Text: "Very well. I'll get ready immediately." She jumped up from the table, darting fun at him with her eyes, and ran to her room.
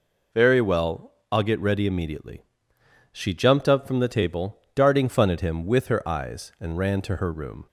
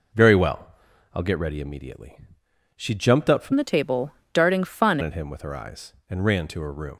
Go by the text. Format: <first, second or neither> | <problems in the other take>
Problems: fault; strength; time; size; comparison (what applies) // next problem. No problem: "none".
first | changes voice from "the" to "fun"; from 3.5 to 4.9 s; 1.4 s long